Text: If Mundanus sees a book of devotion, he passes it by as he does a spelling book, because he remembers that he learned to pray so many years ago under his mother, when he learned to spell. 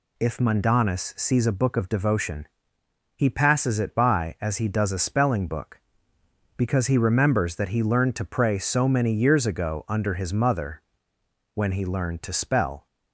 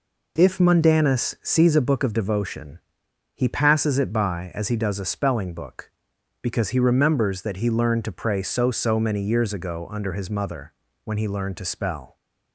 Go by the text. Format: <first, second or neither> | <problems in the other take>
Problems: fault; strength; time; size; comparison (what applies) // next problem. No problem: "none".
first | says "so" twice; at 8.7 s